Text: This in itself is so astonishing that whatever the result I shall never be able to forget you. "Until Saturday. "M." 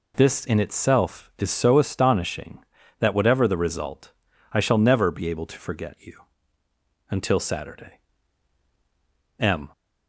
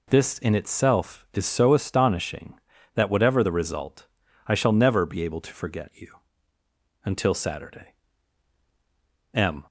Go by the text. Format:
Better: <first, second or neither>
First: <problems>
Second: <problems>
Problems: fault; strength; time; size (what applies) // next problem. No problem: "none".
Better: neither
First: pauses between "result" and "I"; at 4.1 s; 0.42 s long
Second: pauses between "result" and "I"; at 4.0 s; 0.42 s long